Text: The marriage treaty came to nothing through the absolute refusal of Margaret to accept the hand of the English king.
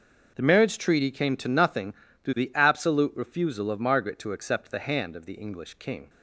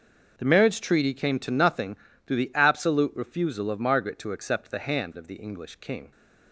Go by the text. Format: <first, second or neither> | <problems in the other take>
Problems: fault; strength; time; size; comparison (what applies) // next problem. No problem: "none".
neither | starts louder than the rest; the same in both // pauses between "nothing" and "through"; slight; the same in both